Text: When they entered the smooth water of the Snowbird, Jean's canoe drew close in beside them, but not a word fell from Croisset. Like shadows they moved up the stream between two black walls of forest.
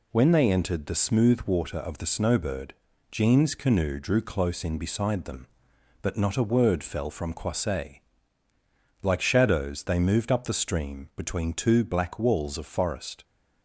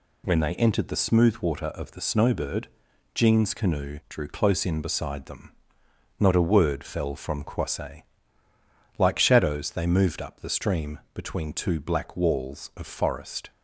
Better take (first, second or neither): first